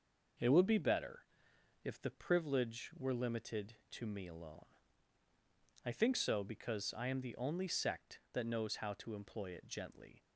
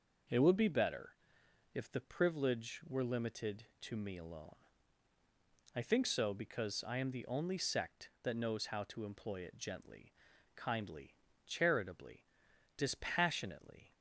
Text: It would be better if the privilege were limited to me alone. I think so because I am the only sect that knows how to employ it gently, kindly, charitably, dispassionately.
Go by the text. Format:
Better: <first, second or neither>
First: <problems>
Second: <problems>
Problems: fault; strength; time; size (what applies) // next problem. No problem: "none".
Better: second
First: pauses between "better" and "if"; noticeable; at 1.2 s; 0.62 s long // stops before "kindly charitably dispassionately"; at 10.2 s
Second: pauses between "better" and "if"; noticeable; at 1.1 s; 0.62 s long